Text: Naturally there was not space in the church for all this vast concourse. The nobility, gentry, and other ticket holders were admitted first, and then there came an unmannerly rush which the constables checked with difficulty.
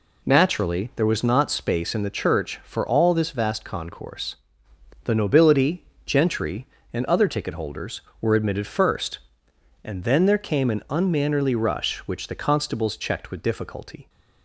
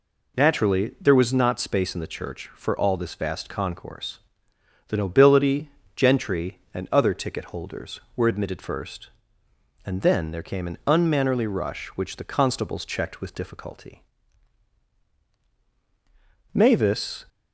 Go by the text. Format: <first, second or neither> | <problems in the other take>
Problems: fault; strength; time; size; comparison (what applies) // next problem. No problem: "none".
first | goes on to say "Mavis"; noticeable; from 16.5 s on; 0.72 s long